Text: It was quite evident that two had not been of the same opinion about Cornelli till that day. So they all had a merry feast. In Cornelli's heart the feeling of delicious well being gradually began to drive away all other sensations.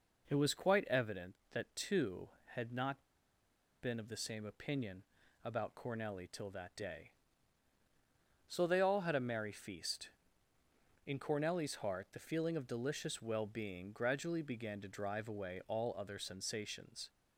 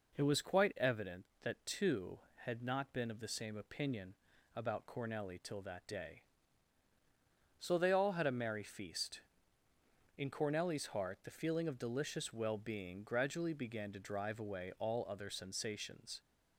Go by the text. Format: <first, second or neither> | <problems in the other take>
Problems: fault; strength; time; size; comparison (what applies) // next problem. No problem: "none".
second | pauses between "not" and "been"; noticeable; at 3.0 s; 0.80 s long // pauses between "opinion" and "about"; at 5.0 s; 0.40 s long; also in the second